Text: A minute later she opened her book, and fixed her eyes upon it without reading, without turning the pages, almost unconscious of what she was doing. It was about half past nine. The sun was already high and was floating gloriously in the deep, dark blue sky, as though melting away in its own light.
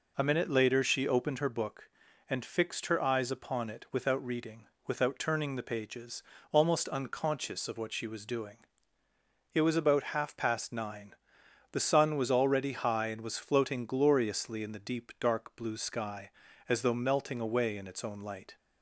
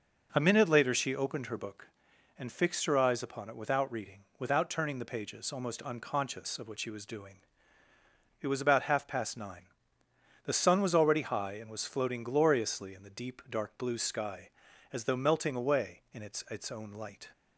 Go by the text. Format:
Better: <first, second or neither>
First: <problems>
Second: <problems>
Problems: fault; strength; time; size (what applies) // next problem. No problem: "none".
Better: first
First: none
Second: says "its" twice; at 16.4 s